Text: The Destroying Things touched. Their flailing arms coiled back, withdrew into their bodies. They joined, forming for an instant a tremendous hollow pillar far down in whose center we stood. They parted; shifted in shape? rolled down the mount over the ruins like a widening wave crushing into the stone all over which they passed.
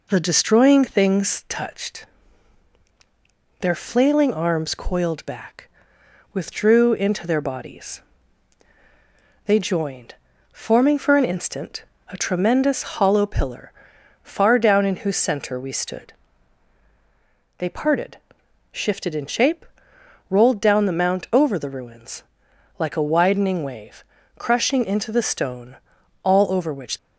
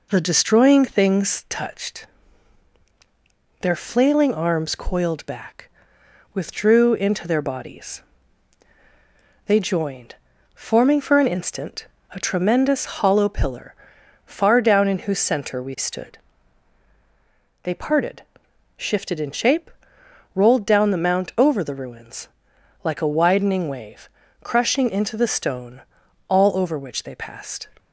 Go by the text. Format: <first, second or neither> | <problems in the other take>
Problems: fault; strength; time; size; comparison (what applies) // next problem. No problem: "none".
second | pauses between "instant" and "a"; slight; at 11.8 s; 0.22 s long; slight in the second // pauses between "pillar" and "far"; noticeable; at 13.7 s; 0.50 s long; noticeable in the second // pauses between "ruins" and "like"; noticeable; at 22.2 s; 0.56 s long; noticeable in the second // pauses between "wave" and "crushing"; slight; at 24.0 s; 0.34 s long; slight in the second // pauses between "stone" and "all"; at 25.7 s; 0.44 s long; also in the second // stops before "they passed"; at 26.9 s